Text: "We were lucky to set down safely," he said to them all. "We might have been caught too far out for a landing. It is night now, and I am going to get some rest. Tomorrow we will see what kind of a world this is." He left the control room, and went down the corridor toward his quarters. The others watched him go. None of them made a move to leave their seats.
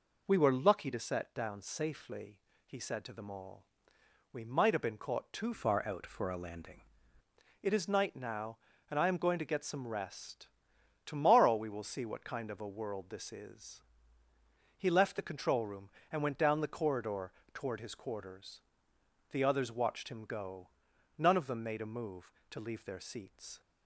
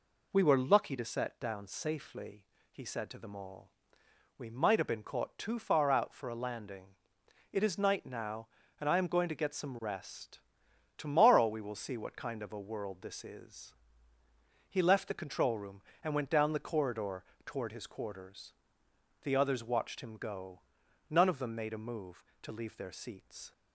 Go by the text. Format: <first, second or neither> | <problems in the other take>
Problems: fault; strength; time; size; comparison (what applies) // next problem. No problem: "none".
second | changes voice from "far" to "landing"; from 5.5 to 6.8 s; 1.3 s long // pauses between "corridor" and "toward"; slight; at 17.3 s; 0.20 s long; slight in the second